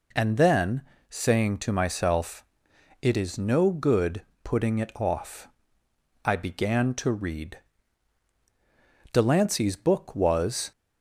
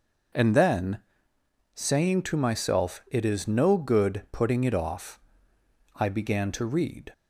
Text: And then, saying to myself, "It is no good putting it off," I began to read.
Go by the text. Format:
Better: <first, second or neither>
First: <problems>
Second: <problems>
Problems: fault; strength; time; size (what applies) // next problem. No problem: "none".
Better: second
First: pauses between "good" and "putting"; slight; at 4.2 s; 0.22 s long // goes on to say "Delancey's book was"; from 9.1 s on; 1.5 s long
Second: none